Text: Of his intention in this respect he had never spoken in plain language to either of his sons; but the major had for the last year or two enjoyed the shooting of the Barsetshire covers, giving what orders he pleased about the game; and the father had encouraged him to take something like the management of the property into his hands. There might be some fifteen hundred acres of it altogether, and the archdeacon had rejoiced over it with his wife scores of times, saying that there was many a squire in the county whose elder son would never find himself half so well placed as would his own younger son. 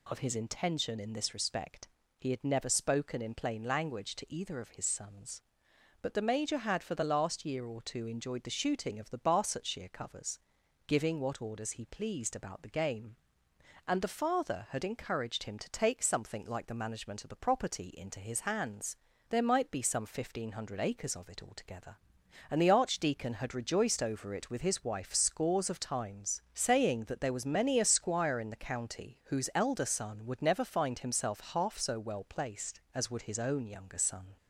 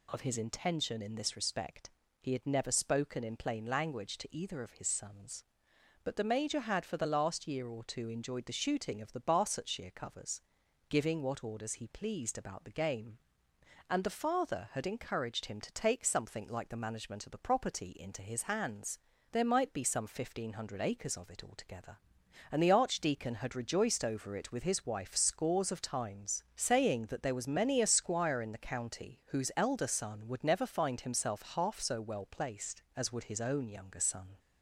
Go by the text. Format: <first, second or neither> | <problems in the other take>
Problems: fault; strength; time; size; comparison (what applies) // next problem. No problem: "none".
neither | pauses between "respect" and "he"; slight; the same in both